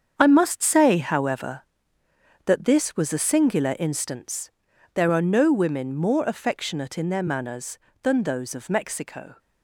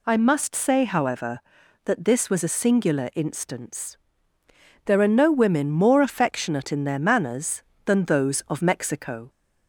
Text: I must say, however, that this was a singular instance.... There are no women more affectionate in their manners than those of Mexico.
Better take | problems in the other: second | gets quieter; strong; throughout; 10 dB

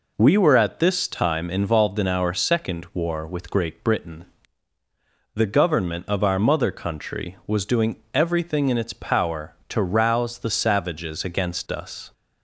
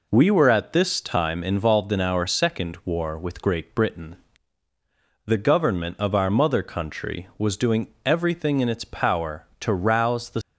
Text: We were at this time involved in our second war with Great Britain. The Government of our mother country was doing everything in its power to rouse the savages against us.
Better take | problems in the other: first | pauses between "doing" and "everything"; slight; at 7.8 s; 0.16 s long; slight in the first // stops before "savages against us"; at 10.4 s

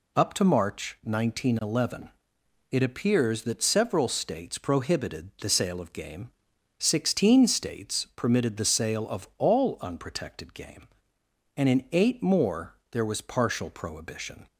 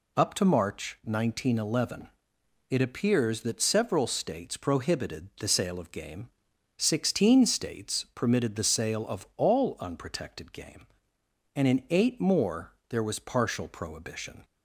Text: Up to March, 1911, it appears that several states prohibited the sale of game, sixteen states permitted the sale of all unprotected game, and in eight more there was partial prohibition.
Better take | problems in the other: neither | pauses between "more" and "there"; slight; the same in both

